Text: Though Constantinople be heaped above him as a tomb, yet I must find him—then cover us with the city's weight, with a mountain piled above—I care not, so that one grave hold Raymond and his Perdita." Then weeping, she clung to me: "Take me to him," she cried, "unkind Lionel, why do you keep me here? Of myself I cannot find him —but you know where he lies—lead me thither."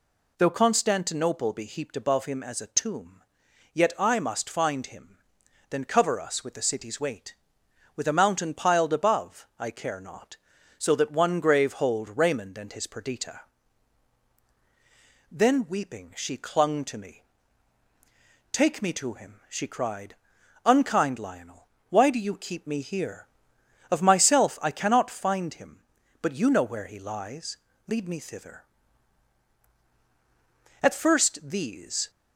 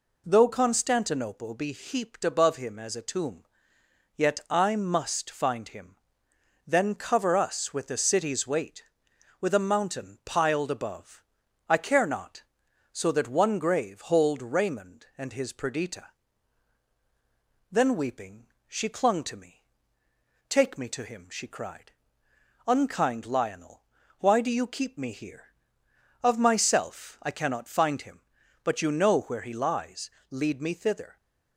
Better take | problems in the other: second | goes on to say "At first these"; noticeable; from 30.8 s on; 1.2 s long

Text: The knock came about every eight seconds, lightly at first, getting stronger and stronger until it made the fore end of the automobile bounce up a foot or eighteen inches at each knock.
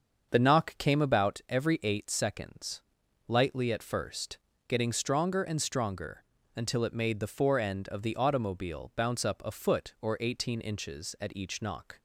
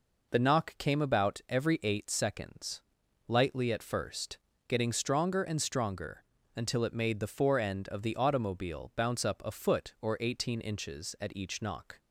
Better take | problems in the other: second | starts louder than the rest; until 1.2 s; 6.5 dB // pauses between "stronger" and "until"; slight; at 6.2 s; 0.34 s long; slight in the second

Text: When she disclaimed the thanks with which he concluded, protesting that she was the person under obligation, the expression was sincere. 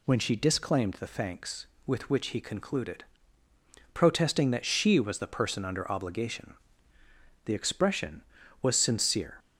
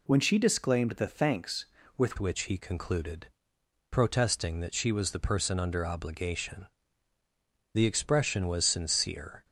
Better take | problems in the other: first | changes voice at "which"; from 2.1 s on; 7.3 s long

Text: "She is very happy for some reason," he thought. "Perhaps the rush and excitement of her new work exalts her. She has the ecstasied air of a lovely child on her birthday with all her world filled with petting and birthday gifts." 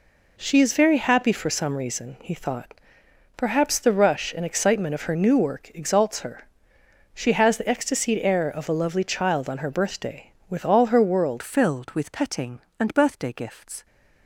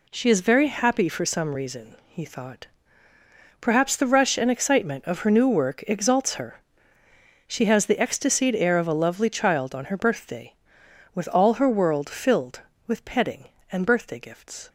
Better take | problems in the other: second | changes voice at "filled"; from 11.4 s on; 2.4 s long

